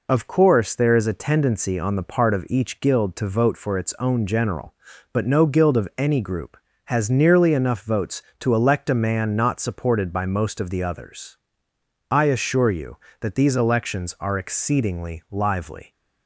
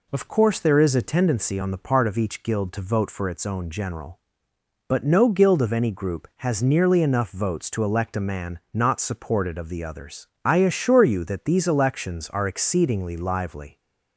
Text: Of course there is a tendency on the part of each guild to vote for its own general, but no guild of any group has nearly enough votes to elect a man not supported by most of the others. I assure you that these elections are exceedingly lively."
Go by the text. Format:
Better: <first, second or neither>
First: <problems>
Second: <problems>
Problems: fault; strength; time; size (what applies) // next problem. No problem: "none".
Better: first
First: none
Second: skips "by most"; at 9.5 s